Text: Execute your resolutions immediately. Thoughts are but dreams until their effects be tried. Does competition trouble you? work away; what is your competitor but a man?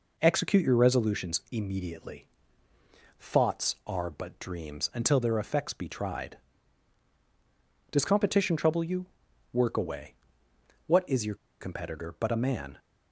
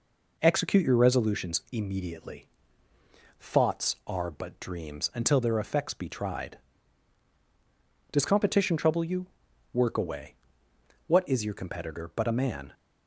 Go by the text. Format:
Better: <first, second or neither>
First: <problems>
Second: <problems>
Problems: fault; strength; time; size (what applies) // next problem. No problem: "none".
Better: second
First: pauses between "your" and "competitor"; slight; at 11.3 s; 0.25 s long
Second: none